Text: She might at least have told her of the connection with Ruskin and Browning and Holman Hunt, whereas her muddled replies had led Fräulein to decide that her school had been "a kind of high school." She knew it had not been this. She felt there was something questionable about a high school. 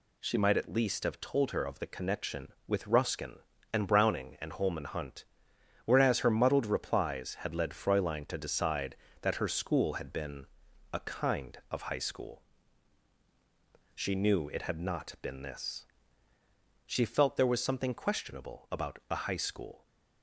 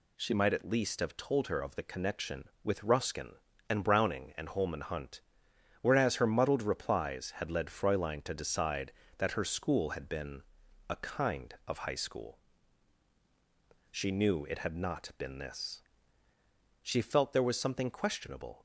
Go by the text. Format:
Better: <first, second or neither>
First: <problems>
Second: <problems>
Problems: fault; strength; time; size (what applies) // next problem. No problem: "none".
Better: first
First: pauses between "been" and "a"; noticeable; at 10.4 s; 0.46 s long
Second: pauses between "been" and "a"; noticeable; at 10.4 s; 0.46 s long // stops before "about a high school"; at 18.5 s